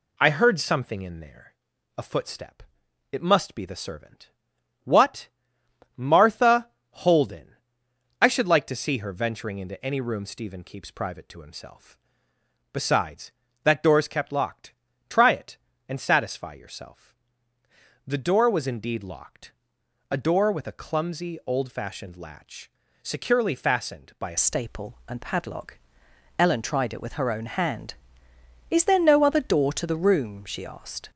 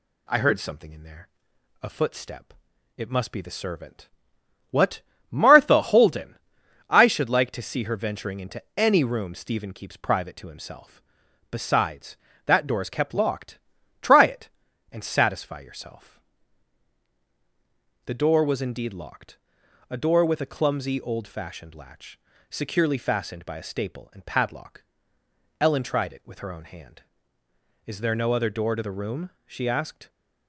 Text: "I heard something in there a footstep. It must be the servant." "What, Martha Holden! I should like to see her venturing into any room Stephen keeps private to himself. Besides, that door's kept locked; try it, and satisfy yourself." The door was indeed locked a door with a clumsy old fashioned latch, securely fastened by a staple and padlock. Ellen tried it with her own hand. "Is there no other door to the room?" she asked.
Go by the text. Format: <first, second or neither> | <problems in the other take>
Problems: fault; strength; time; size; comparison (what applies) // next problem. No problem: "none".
second | pauses between "there" and "a"; at 1.5 s; 0.44 s long; noticeable in the second // pauses between "Martha" and "Holden"; slight; at 6.6 s; 0.22 s long // pauses between "locked" and "a"; noticeable; at 19.5 s; 0.60 s long; noticeable in the second // changes voice at "staple"; from 24.3 s on; 6.8 s long